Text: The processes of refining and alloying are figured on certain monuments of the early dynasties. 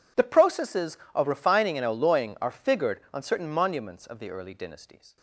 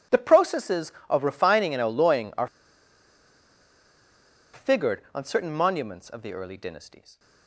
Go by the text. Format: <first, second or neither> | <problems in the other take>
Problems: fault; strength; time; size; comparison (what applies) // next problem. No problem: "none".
first | pauses between "are" and "figured"; strong; at 2.4 s; 2.0 s long